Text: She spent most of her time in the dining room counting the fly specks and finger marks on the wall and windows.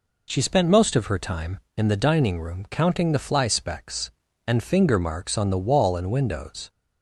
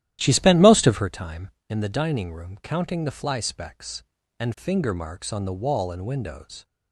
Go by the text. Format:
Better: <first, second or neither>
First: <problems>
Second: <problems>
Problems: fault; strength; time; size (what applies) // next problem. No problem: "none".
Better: first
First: none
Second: starts louder than the rest; strong; until 1.1 s; 13 dB